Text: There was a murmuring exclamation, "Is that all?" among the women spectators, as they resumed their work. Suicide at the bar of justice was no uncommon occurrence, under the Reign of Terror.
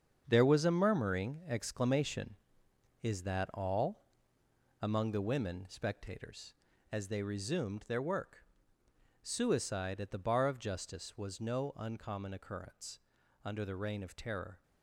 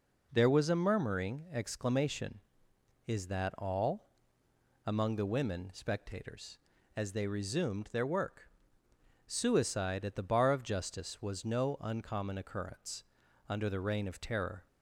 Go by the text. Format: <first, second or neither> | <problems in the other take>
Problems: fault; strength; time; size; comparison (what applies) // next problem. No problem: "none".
second | gets quieter; strong; throughout; 9.5 dB